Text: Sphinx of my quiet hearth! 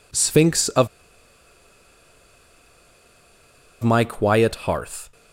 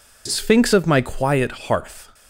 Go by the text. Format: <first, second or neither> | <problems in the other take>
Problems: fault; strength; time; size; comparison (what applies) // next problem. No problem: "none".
second | pauses between "of" and "my"; strong; at 0.8 s; 2.9 s long